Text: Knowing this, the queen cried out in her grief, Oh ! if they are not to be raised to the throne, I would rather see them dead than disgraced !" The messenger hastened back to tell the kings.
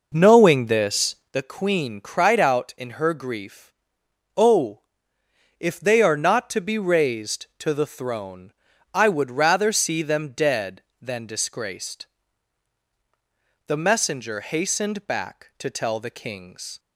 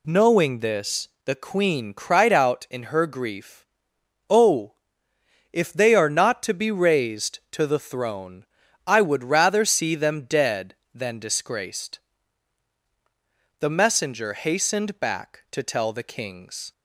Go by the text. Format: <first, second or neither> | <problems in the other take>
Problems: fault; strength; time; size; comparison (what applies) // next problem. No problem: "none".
second | starts louder than the rest; noticeable; until 1.4 s; 5 dB